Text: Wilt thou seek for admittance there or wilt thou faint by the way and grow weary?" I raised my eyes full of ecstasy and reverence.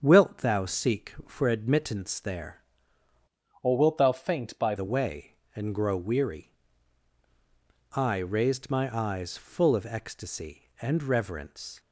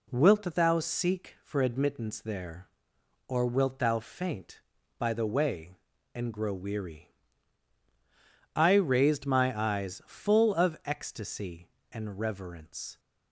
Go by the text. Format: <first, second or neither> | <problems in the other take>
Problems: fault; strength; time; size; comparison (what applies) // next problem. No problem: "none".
second | starts louder than the rest; strong; until 1.0 s; 7 dB // changes voice from "or" to "by"; from 3.6 to 4.7 s; 1.1 s long